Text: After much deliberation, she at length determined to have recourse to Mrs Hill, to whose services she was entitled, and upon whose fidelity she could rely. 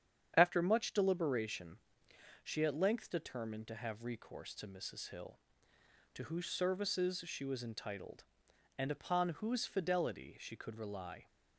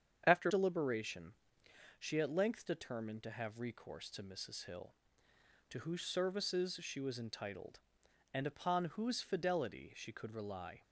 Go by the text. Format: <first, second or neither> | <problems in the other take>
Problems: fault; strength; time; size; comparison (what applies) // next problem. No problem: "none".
first | starts louder than the rest; strong; until 1.2 s; 8 dB; strong in the first // skips "much"; at 0.4 s